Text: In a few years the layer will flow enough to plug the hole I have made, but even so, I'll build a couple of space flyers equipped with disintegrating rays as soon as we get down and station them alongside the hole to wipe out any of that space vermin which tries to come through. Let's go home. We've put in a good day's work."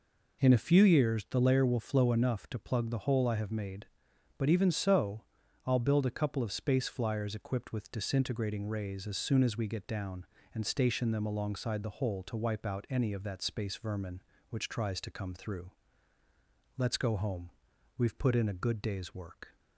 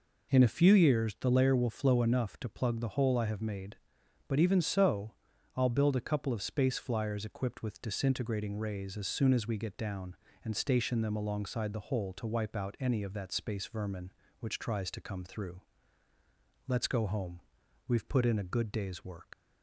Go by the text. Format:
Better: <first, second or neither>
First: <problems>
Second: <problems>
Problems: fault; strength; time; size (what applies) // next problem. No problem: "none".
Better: first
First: none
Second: leaves "work" unfinished; at 19.3 s; 155 ms